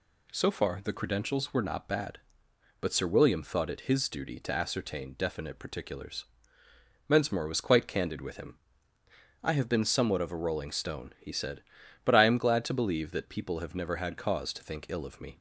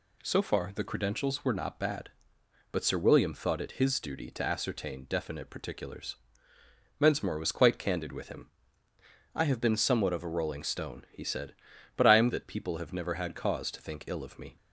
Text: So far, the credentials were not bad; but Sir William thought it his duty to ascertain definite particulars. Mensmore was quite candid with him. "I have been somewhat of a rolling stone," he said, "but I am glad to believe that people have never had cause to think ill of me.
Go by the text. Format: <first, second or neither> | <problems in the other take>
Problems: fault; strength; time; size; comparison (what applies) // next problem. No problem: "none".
first | skips "glad to believe"; at 12.2 s